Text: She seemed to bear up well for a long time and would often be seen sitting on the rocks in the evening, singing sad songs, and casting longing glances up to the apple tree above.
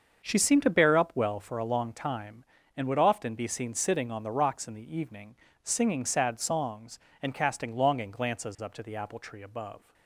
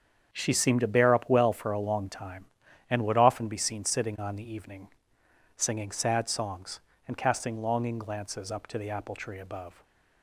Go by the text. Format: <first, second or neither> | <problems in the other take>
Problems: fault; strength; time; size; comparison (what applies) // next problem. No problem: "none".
first | starts louder than the rest; strong; until 1.3 s; 7.5 dB; also in the first // skips "rocks in the"; at 4.5 s // stays silent after the last word; slight; from 9.7 s on; 0.5 s long